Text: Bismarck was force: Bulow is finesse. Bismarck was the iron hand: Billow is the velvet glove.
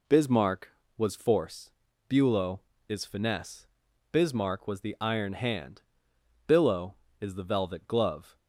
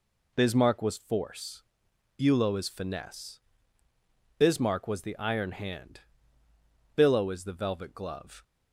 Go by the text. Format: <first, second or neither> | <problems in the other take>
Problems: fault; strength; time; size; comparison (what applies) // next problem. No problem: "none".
neither | none